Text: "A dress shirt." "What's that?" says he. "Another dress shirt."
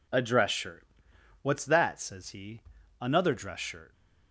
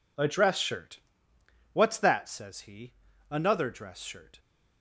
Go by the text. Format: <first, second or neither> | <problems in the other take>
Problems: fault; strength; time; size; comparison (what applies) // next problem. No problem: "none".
neither | none